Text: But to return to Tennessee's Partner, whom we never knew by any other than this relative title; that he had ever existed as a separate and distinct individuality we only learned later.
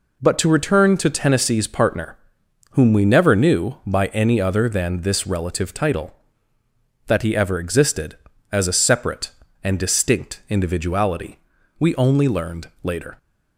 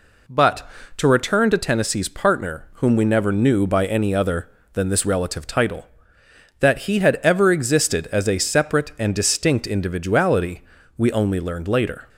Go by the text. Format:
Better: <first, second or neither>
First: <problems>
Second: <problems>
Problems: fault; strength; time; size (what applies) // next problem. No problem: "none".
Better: second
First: skips "had"; at 7.3 s // pauses between "individuality" and "we"; at 11.3 s; 0.42 s long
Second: pauses between "individuality" and "we"; slight; at 10.6 s; 0.34 s long